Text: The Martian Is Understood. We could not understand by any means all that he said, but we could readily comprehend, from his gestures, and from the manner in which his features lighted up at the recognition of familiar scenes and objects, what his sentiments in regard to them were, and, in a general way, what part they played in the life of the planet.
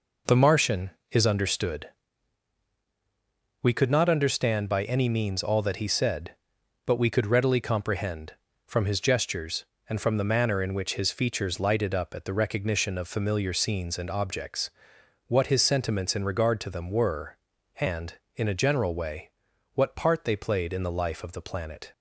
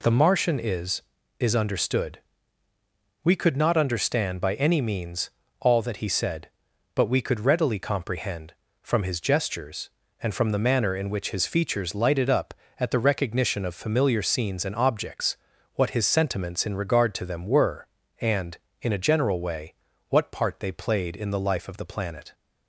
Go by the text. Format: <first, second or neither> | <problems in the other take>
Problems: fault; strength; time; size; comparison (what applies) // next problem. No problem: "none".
first | says "Is" twice; at 1.3 s // pauses between "means" and "all"; slight; at 5.2 s; 0.30 s long